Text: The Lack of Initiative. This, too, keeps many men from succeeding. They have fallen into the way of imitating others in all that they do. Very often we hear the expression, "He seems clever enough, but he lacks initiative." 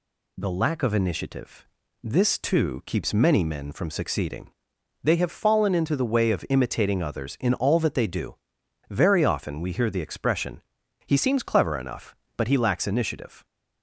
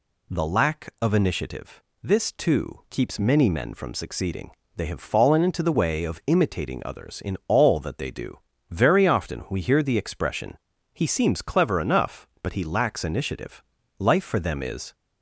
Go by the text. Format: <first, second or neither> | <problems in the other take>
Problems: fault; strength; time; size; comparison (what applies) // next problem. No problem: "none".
first | goes on to say "Life for them is"; noticeable; from 13.9 s on; 0.96 s long